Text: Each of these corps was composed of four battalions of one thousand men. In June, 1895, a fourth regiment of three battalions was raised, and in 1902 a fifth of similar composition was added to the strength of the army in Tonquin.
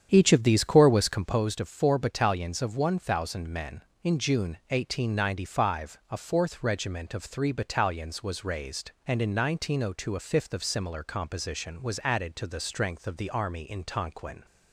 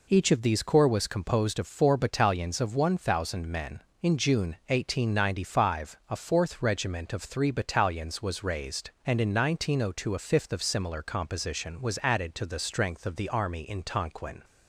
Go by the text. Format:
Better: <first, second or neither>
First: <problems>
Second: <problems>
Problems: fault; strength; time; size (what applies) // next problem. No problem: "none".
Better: second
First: starts louder than the rest; strong; until 1.4 s; 8.5 dB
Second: none